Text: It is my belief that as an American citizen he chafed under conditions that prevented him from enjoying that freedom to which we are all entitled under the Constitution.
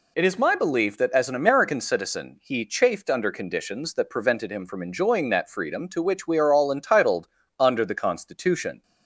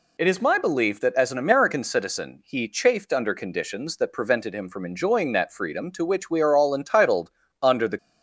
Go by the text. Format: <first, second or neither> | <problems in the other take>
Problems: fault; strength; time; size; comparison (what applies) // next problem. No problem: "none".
first | pauses between "entitled" and "under"; slight; at 7.3 s; 0.32 s long; slight in the first // stops before "Constitution"; at 7.9 s